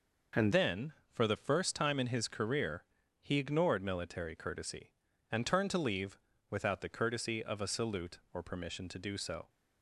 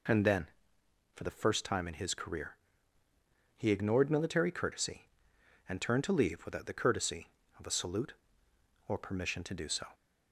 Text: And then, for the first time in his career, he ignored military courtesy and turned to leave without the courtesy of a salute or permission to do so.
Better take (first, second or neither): second